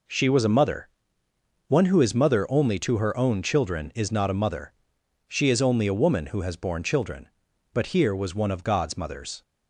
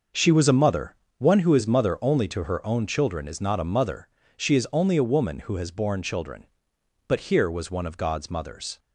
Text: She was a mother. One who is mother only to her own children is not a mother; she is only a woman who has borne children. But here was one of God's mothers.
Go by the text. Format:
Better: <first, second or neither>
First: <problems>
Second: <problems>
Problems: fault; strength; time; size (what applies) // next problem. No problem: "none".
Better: neither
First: none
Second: none